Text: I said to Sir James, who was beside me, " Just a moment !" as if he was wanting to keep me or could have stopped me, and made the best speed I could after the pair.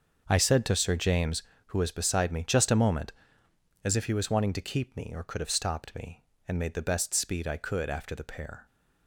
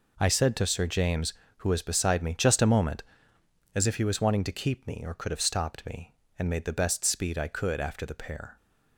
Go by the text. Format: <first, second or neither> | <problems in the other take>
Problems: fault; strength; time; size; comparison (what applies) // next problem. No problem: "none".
second | starts louder than the rest; until 1.4 s; 6 dB